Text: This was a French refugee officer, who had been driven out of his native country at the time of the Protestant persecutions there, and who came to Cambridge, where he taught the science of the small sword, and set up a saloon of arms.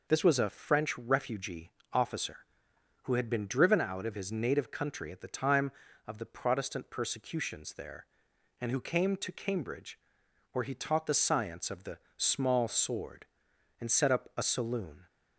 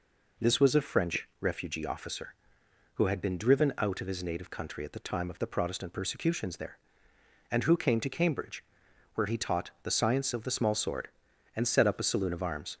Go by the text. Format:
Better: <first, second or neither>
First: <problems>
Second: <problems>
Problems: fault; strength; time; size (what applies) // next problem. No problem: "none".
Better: second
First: pauses between "refugee" and "officer"; slight; at 1.7 s; 0.22 s long // pauses between "the" and "small"; slight; at 11.9 s; 0.18 s long // stops before "of arms"; at 15.0 s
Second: none